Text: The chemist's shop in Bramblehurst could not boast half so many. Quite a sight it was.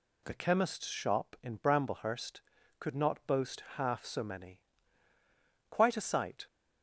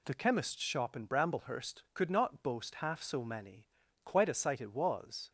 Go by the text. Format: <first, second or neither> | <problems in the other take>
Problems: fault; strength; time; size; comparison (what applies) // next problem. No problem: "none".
second | stops before "it was"; at 6.4 s